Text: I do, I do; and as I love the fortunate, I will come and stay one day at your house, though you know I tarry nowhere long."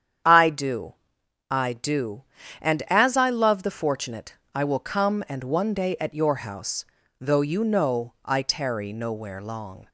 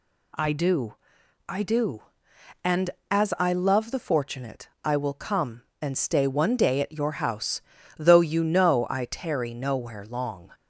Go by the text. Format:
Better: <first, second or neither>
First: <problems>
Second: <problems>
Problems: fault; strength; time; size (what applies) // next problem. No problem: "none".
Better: second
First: starts louder than the rest; strong; until 1.8 s; 9 dB // skips "stay"; at 5.4 s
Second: none